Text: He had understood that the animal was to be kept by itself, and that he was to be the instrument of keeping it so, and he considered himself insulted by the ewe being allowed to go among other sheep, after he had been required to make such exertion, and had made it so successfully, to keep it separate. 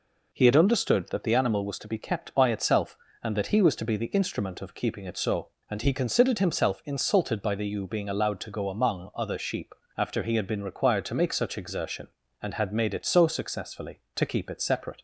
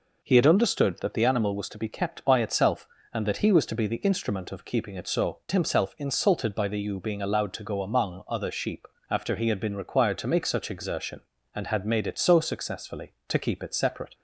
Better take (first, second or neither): first